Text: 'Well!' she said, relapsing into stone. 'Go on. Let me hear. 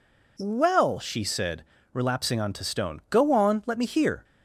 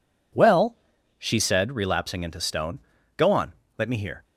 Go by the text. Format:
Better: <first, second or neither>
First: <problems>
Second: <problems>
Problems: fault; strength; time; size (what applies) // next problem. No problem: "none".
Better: second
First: says "onto" for "into"; at 2.3 s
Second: none